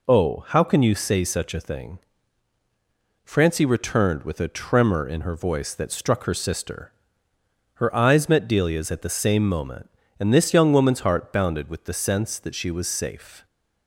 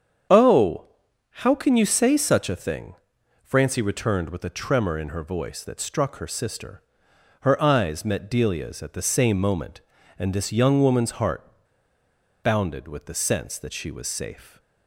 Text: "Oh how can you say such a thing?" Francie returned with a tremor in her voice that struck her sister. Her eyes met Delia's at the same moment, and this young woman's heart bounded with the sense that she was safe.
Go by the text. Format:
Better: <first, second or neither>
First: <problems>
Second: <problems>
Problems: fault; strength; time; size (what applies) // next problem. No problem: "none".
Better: first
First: none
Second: starts louder than the rest; strong; until 1.8 s; 8 dB // pauses between "Oh" and "how"; noticeable; at 0.8 s; 0.52 s long // pauses between "heart" and "bounded"; at 11.4 s; 1.0 s long